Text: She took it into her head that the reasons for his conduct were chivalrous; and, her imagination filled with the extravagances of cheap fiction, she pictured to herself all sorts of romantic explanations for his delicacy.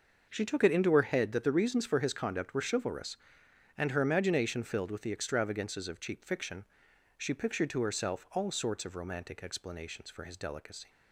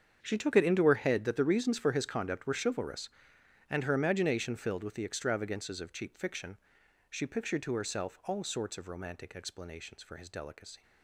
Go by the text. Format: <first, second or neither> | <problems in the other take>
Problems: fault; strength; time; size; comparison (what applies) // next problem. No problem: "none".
first | gets quieter; strong; throughout; 15 dB